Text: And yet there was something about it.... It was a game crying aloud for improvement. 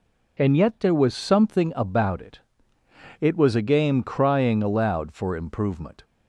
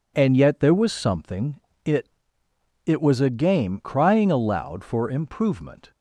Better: first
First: none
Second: skips "about"; at 1.7 s

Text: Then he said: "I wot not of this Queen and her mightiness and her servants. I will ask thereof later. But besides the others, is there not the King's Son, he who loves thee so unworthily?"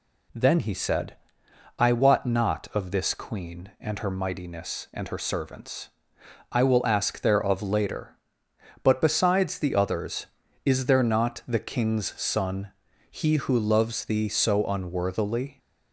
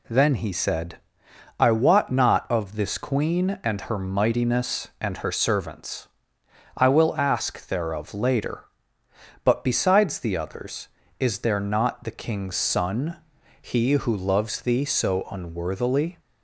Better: neither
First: none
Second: none

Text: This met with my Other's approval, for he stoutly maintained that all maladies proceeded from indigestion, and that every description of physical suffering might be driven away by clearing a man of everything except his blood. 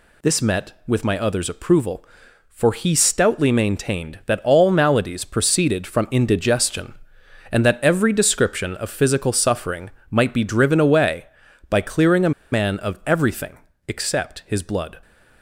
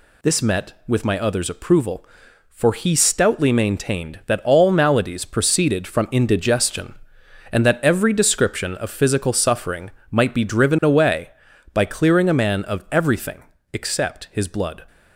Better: second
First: pauses between "suffering" and "might"; slight; at 9.9 s; 0.20 s long // pauses between "a" and "man"; slight; at 12.3 s; 0.21 s long // pauses between "everything" and "except"; slight; at 13.5 s; 0.30 s long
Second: pauses between "suffering" and "might"; slight; at 9.9 s; 0.20 s long // pauses between "everything" and "except"; slight; at 13.4 s; 0.30 s long

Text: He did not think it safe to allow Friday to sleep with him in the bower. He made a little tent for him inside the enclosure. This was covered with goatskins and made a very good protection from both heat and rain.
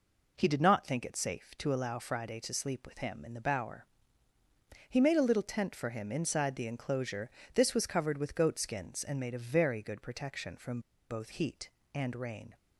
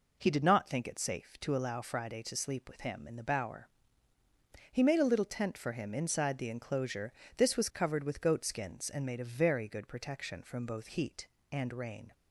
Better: second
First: pauses between "from" and "both"; slight; at 10.7 s; 0.31 s long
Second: none

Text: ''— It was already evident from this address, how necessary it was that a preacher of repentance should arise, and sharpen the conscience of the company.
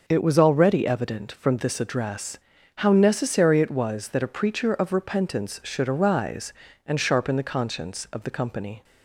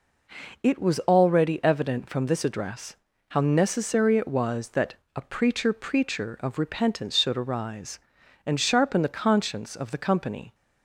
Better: first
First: none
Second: pauses between "that" and "a"; slight; at 4.9 s; 0.20 s long // says "preacher" twice; at 5.7 s

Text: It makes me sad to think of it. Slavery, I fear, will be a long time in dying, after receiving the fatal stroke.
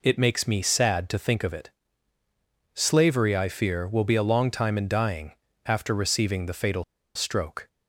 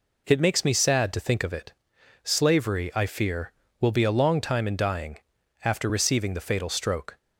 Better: second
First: pauses between "fatal" and "stroke"; slight; at 6.8 s; 0.31 s long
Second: none

